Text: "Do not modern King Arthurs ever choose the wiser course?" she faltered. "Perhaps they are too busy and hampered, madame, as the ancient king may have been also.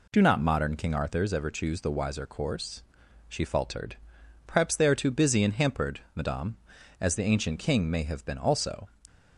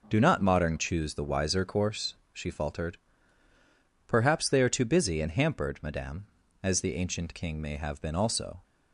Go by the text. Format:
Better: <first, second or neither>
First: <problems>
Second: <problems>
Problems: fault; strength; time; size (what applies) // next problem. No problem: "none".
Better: first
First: none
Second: skips "King Arthurs ever"; at 0.7 s